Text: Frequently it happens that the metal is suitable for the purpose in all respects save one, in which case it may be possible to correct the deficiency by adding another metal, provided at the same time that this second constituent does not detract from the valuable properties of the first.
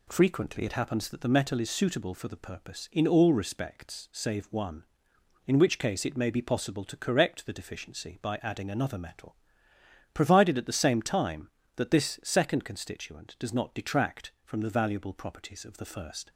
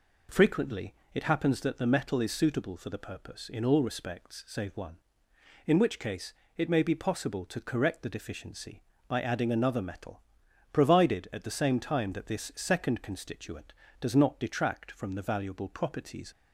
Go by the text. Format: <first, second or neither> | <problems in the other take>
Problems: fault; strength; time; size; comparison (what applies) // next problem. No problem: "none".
first | pauses between "Frequently" and "it"; slight; at 0.9 s; 0.18 s long // pauses between "case" and "it"; slight; at 6.3 s; 0.22 s long // stops before "of the first"; at 16.3 s